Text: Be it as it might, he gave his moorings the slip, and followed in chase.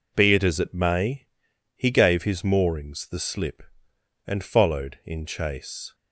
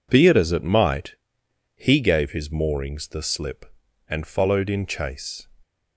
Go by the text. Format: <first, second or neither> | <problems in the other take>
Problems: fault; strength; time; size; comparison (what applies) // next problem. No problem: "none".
second | says "may" for "might"; at 0.7 s